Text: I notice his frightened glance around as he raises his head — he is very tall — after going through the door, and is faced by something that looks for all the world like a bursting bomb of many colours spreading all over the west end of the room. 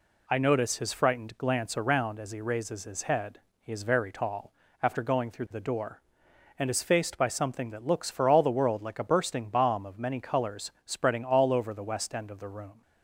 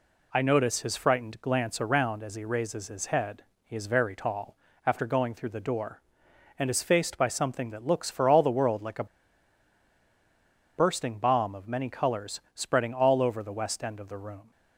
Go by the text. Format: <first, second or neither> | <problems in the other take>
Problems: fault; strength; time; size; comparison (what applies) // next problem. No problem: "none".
first | pauses between "a" and "bursting"; strong; at 9.0 s; 1.7 s long